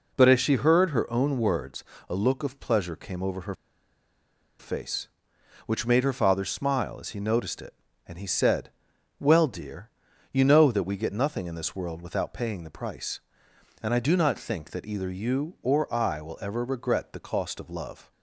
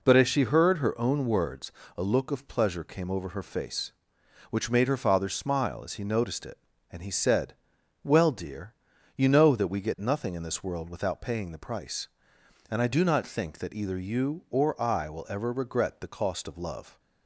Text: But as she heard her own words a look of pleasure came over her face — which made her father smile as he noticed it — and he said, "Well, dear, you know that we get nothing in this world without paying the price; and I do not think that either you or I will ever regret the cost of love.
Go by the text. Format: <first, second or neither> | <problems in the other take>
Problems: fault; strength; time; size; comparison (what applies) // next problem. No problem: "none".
second | pauses between "words" and "a"; slight; at 1.8 s; 0.24 s long; slight in the second // pauses between "her" and "face"; at 3.5 s; 1.0 s long